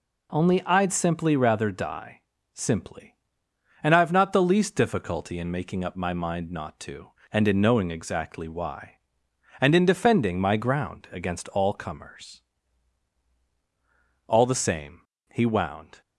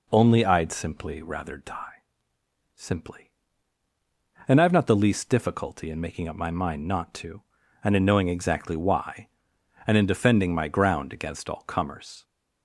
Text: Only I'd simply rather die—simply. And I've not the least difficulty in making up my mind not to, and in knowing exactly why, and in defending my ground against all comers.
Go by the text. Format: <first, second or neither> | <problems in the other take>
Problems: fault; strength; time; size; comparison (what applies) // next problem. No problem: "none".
second | goes on to say "All the same he wound"; strong; from 14.2 s on; 1.7 s long